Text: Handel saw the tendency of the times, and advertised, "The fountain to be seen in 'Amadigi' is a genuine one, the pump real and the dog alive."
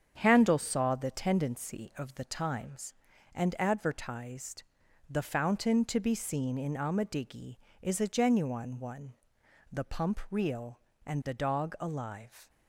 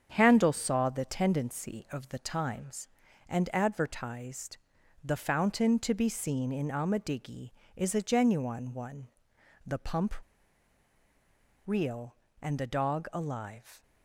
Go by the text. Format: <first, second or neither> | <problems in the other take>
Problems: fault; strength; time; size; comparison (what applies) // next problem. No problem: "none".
first | starts louder than the rest; strong; until 1.1 s; 7.5 dB; strong in the first // pauses between "pump" and "real"; strong; at 10.1 s; 1.5 s long